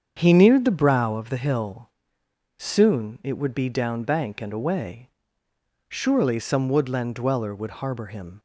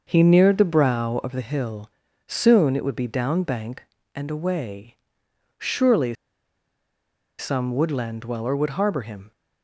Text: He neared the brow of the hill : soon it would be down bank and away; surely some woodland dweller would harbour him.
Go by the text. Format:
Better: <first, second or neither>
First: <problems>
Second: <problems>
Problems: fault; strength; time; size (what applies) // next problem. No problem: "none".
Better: first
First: starts louder than the rest; strong; until 1.1 s; 7.5 dB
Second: starts louder than the rest; until 1.0 s; 6 dB // pauses between "surely" and "some"; strong; at 6.1 s; 1.2 s long